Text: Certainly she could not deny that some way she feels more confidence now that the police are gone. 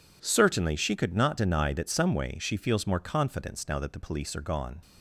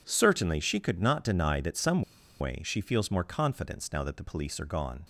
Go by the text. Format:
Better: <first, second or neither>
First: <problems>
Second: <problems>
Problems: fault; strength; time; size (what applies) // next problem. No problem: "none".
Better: first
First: none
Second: pauses between "some" and "way"; at 2.0 s; 0.37 s long